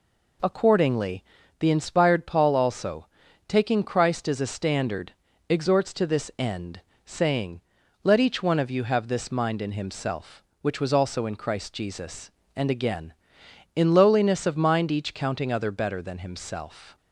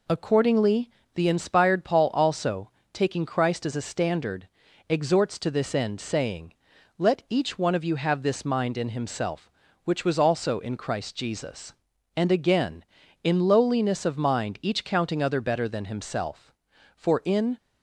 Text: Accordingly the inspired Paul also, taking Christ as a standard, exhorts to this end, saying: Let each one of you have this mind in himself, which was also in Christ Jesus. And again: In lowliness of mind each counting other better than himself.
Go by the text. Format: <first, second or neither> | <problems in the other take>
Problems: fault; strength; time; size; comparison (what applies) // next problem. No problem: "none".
first | pauses between "Accordingly" and "the"; slight; at 0.8 s; 0.26 s long; slight in the first // goes on to say "For in"; noticeable; from 16.9 s on; 0.62 s long